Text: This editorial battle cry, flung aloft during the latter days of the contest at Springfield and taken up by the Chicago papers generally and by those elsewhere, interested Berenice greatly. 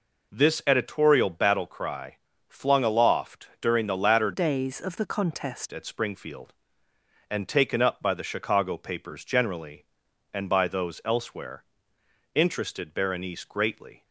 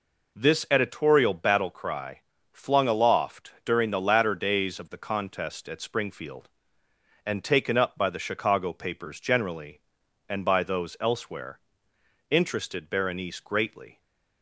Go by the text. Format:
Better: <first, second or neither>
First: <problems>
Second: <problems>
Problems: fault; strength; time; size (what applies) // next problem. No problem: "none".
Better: second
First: changes voice from "days" to "contest"; from 4.3 to 5.7 s; 1.4 s long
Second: none